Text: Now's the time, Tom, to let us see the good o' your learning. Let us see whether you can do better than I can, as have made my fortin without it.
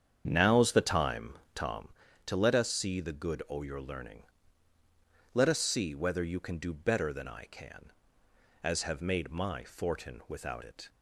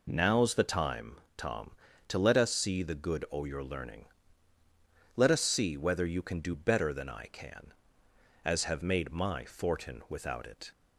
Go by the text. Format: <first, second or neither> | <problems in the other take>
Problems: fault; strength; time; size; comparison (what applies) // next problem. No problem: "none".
second | starts louder than the rest; strong; until 1.8 s; 8 dB